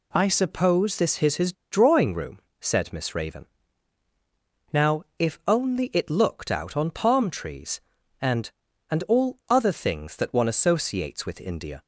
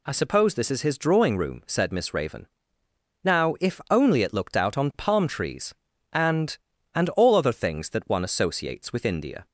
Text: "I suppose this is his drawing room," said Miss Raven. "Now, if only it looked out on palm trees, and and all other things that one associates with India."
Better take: second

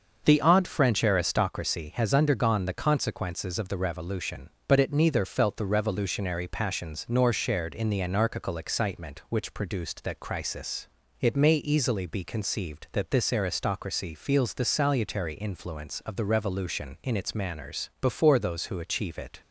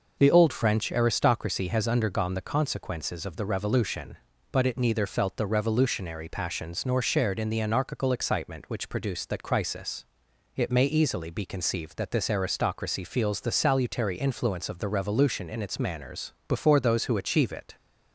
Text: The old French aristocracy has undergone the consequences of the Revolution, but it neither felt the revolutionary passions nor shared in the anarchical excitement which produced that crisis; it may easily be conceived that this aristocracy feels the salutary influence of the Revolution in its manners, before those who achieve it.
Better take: second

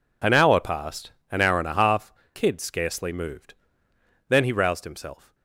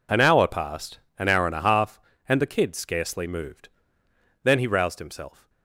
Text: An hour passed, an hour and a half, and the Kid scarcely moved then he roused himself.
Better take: second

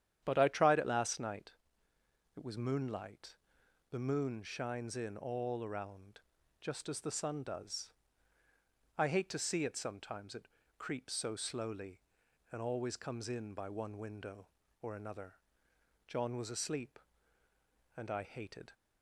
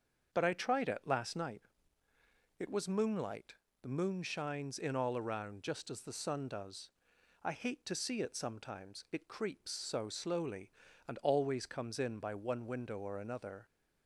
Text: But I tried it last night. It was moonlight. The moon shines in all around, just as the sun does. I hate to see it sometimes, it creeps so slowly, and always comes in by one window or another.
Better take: second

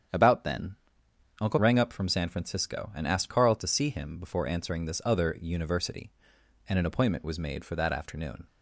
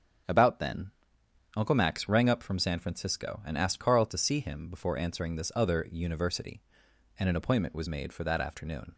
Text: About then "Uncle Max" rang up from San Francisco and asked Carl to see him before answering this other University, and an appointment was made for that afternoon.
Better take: second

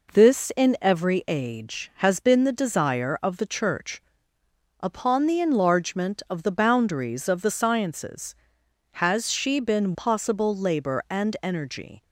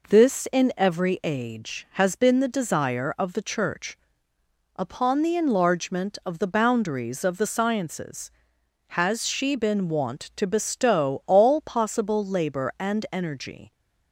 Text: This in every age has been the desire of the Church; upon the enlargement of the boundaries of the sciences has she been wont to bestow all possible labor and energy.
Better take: second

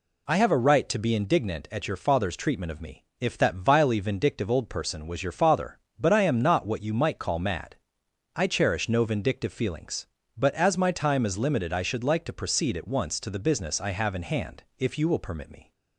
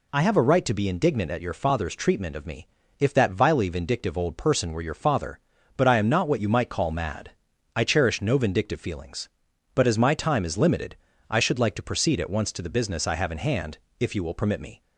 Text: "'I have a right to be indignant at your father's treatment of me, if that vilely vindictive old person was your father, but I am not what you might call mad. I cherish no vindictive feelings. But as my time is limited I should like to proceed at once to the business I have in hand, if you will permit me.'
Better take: first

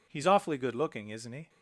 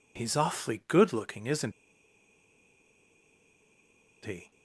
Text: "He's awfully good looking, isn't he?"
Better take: first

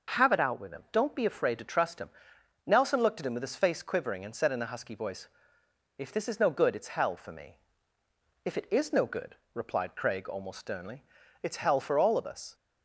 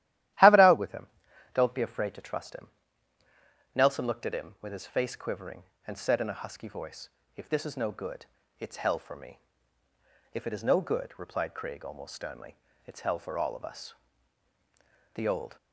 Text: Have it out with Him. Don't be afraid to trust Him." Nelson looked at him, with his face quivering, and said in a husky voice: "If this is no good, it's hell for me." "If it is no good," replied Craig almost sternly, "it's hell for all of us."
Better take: first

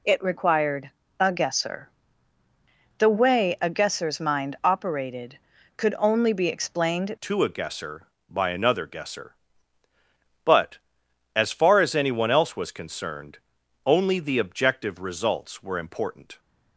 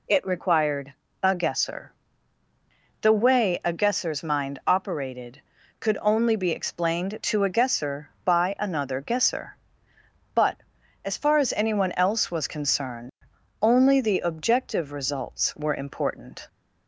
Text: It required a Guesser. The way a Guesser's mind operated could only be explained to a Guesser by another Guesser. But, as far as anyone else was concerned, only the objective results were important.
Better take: second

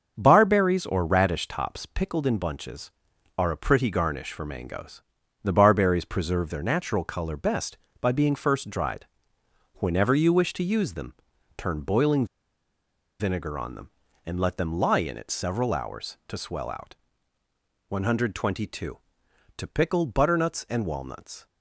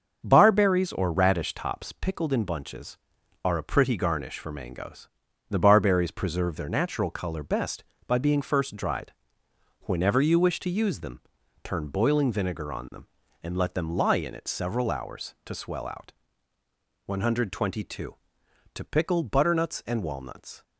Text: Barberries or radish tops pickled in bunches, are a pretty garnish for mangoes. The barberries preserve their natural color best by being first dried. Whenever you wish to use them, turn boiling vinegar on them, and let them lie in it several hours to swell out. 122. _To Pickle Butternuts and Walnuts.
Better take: second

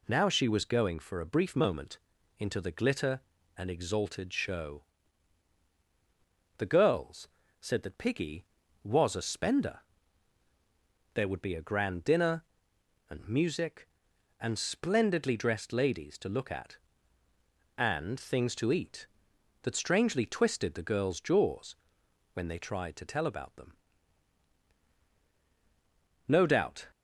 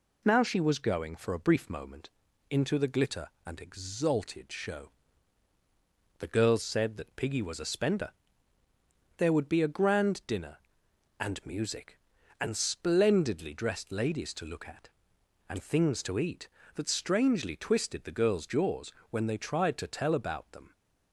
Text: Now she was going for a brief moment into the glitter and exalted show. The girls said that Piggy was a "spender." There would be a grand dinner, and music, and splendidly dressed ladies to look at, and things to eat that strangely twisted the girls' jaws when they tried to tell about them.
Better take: second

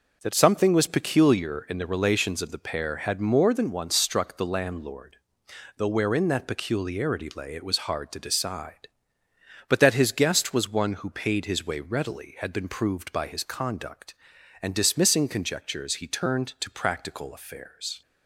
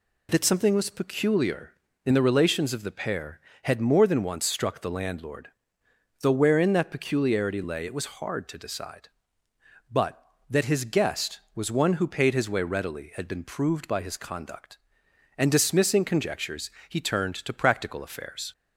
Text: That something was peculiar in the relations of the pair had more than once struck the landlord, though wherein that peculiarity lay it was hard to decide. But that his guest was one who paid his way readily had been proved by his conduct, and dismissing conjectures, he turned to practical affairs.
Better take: neither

